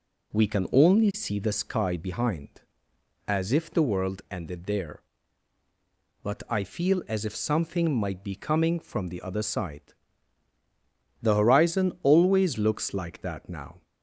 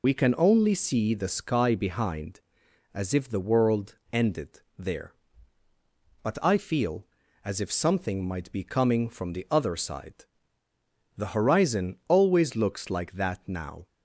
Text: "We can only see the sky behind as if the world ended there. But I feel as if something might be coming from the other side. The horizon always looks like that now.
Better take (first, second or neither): first